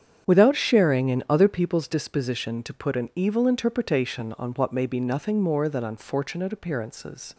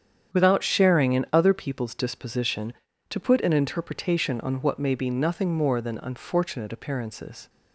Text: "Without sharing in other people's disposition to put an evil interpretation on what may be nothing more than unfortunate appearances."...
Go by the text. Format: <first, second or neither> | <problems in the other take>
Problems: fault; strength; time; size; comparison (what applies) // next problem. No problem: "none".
first | starts louder than the rest; strong; until 1.4 s; 8.5 dB; strong in the first // skips "evil"; at 3.5 s